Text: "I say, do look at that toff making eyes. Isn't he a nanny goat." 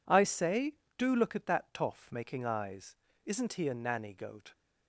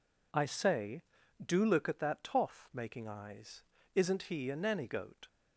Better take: neither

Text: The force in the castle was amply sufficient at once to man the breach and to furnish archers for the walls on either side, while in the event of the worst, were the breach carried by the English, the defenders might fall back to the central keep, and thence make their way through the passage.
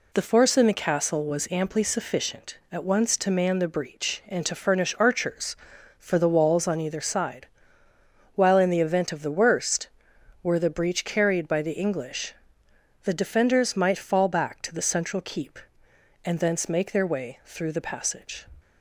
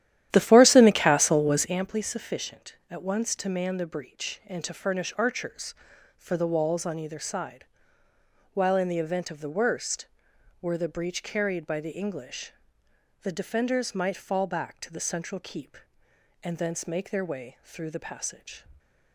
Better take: first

